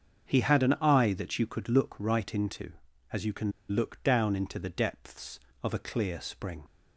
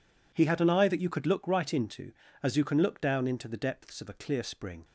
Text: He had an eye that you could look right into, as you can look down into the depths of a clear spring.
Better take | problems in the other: second | starts louder than the rest; until 1.3 s; 7 dB // pauses between "can" and "look"; slight; at 3.5 s; 0.18 s long

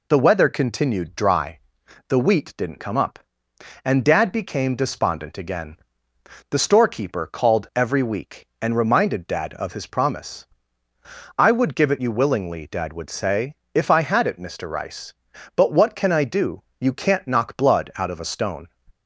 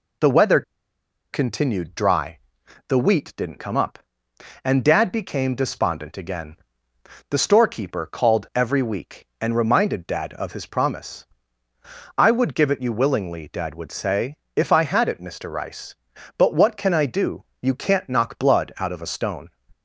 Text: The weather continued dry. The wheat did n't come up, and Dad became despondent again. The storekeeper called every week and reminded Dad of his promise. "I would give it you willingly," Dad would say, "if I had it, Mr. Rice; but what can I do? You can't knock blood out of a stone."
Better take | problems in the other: first | pauses between "weather" and "continued"; noticeable; at 0.6 s; 0.71 s long

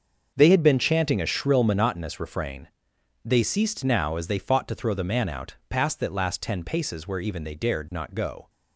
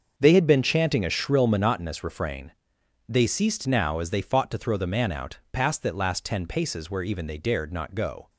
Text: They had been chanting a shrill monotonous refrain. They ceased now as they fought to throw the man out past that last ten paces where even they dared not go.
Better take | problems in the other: neither | starts louder than the rest; the same in both

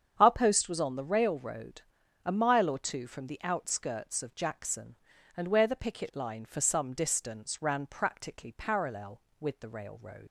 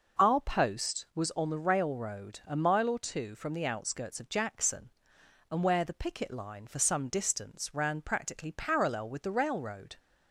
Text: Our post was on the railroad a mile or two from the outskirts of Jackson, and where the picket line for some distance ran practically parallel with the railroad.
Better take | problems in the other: second | starts louder than the rest; strong; until 1.1 s; 8 dB // pauses between "railroad" and "a"; at 1.8 s; 0.42 s long // leaves "railroad" unfinished; at 10.2 s; 95 ms

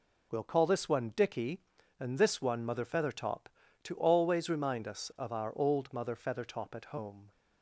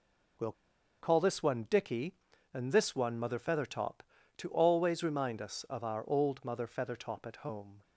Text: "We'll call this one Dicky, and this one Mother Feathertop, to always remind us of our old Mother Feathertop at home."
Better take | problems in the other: first | pauses between "We'll" and "call"; noticeable; at 0.5 s; 0.48 s long

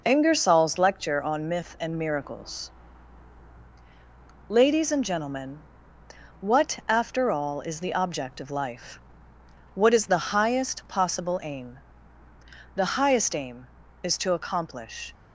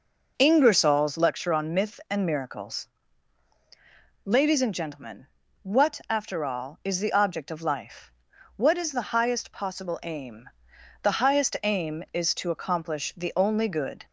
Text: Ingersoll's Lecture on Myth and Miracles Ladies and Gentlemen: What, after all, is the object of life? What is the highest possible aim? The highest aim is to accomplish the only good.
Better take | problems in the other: second | pauses between "Miracles" and "Ladies"; strong; at 2.6 s; 1.8 s long; strong in the second // stops before "the only good"; at 15.1 s

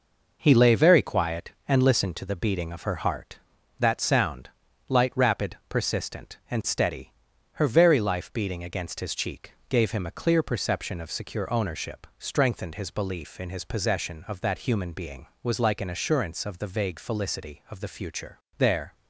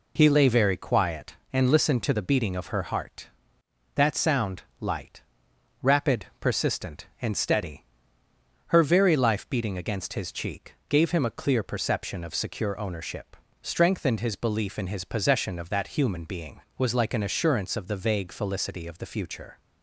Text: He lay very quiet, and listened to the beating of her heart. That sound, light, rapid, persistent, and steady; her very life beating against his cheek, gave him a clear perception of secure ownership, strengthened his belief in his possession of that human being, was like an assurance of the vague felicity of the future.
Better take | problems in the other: second | goes on to say "There"; slight; from 18.5 s on; 0.36 s long

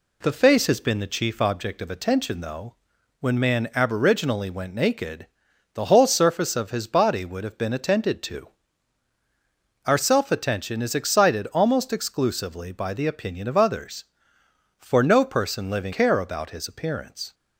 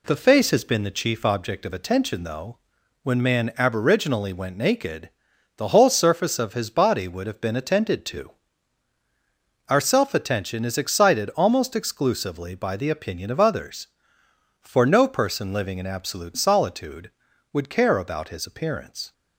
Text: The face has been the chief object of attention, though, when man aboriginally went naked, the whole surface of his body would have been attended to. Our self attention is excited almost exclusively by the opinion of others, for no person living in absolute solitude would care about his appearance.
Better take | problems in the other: second | skips "in absolute solitude would"; at 15.9 s

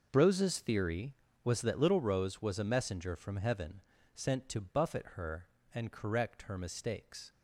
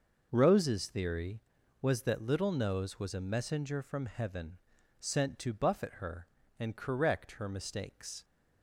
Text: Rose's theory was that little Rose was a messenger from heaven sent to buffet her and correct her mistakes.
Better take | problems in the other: first | says "Nose" for "Rose"; at 2.5 s // pauses between "heaven" and "sent"; at 4.5 s; 0.42 s long; slight in the first

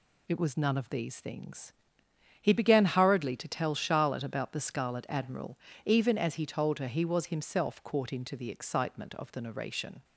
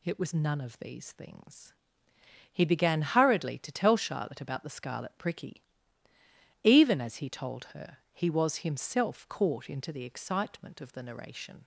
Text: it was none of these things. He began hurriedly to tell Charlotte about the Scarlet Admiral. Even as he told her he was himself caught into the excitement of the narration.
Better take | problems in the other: first | says "Pricky" for "Admiral"; at 5.1 s

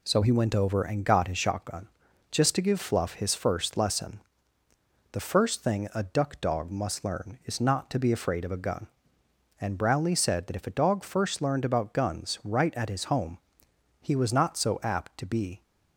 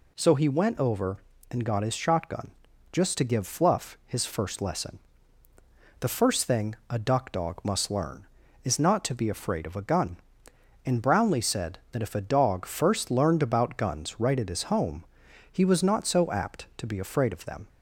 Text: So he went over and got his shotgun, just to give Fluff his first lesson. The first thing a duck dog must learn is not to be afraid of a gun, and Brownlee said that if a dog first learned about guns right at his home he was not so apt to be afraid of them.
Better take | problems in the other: second | pauses between "home" and "he"; noticeable; at 13.3 s; 0.62 s long; noticeable in the second // stops before "afraid of them"; at 15.6 s

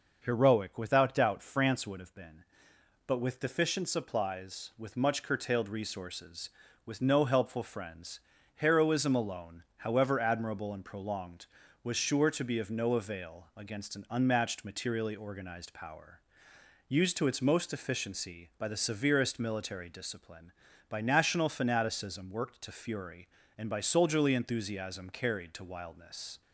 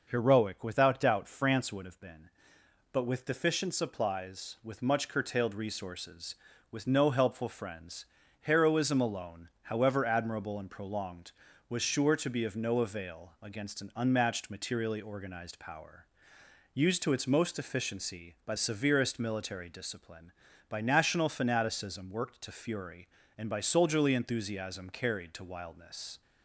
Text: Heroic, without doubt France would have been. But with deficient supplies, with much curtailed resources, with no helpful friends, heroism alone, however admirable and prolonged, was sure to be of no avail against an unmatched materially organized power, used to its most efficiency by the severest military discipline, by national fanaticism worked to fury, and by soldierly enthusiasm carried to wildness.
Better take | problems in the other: first | skips "the"; at 18.5 s

